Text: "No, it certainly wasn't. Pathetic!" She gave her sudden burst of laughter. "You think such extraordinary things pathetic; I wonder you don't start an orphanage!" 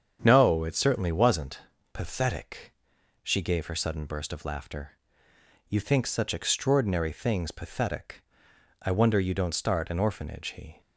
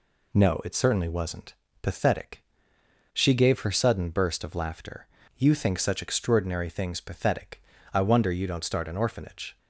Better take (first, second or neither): second